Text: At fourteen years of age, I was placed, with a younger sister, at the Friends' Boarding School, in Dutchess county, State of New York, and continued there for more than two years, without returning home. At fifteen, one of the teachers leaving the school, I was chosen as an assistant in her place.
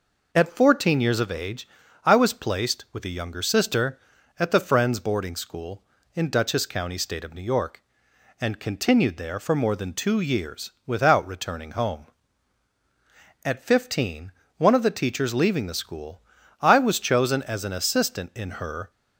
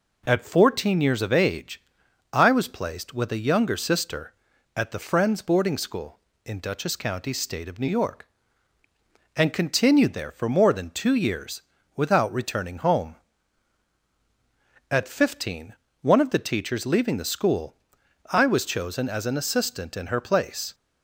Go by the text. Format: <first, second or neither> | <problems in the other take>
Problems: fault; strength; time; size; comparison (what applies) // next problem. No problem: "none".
second | stops before "place"; at 18.9 s